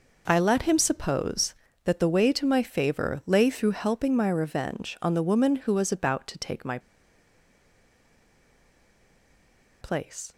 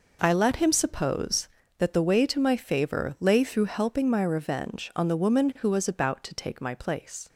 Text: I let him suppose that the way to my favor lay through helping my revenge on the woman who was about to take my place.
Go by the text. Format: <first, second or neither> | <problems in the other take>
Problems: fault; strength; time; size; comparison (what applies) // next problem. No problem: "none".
second | pauses between "my" and "place"; strong; at 6.7 s; 3.0 s long